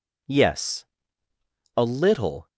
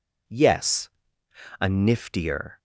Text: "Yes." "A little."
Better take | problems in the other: first | says "niftier" for "little"; at 1.6 s

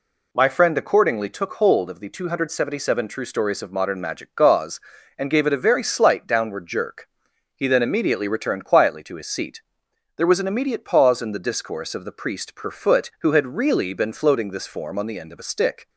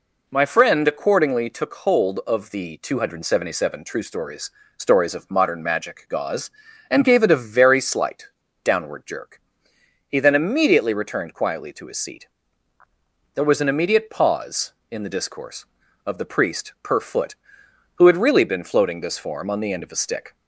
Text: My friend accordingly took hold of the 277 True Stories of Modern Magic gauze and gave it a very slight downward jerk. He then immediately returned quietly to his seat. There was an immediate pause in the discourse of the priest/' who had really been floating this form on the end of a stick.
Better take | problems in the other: first | says "Stories" twice; at 4.7 s // pauses between "slight" and "downward"; at 8.2 s; 0.38 s long

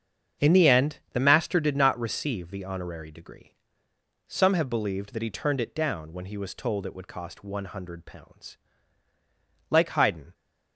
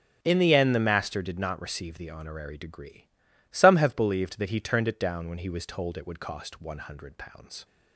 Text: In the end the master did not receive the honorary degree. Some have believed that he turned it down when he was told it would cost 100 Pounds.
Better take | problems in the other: second | starts louder than the rest; strong; until 1.5 s; 7.5 dB; also in the second // goes on to say "Like Haydn"; noticeable; from 9.6 s on; 0.66 s long

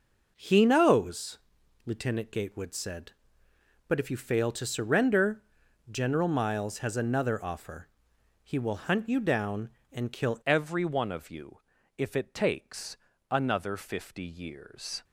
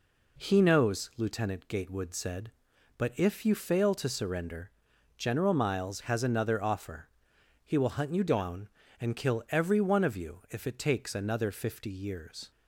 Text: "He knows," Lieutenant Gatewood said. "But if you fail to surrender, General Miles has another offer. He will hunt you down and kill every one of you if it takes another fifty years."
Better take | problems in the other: second | changes voice at "every"; from 10.4 s on; 4.6 s long // pauses between "you" and "if"; slight; at 11.5 s; 0.36 s long // pauses between "takes" and "another"; slight; at 12.9 s; 0.32 s long

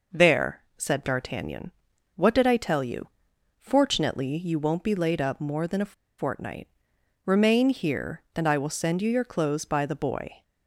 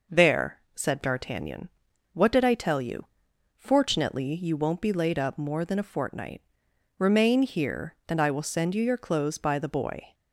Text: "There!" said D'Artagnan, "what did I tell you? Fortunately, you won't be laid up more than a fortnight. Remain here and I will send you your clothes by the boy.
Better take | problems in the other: second | pauses between "a" and "fortnight"; slight; at 5.9 s; 0.25 s long

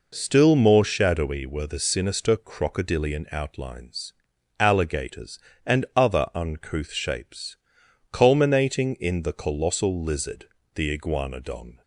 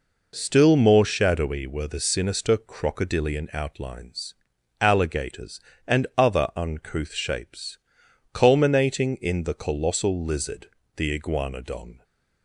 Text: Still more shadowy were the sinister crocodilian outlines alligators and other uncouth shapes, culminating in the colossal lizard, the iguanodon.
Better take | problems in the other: neither | pauses between "outlines" and "alligators"; noticeable; the same in both

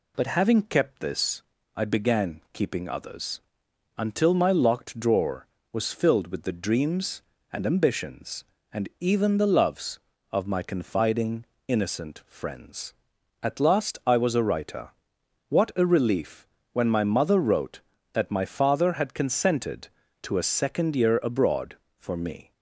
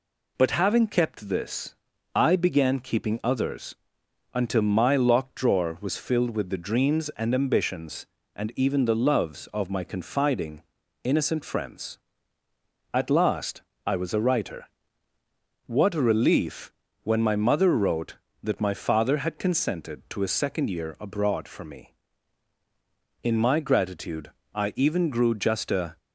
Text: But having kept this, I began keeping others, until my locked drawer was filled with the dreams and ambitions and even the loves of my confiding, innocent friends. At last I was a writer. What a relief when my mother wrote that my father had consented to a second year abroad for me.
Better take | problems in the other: first | pauses between "last" and "I"; slight; at 13.6 s; 0.24 s long // pauses between "relief" and "when"; slight; at 16.7 s; 0.32 s long; slight in the first // goes on to say "In my gratitude I even grew just a"; strong; from 23.2 s on; 2.7 s long

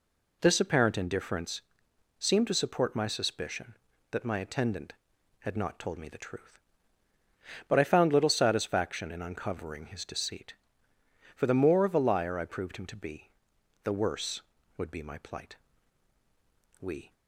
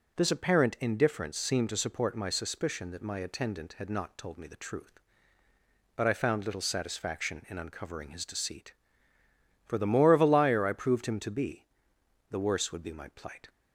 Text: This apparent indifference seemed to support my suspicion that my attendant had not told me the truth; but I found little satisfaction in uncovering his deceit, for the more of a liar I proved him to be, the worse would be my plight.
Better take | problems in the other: second | pauses between "indifference" and "seemed"; noticeable; at 1.6 s; 0.58 s long // goes on to say "We"; slight; from 16.7 s on; 0.34 s long

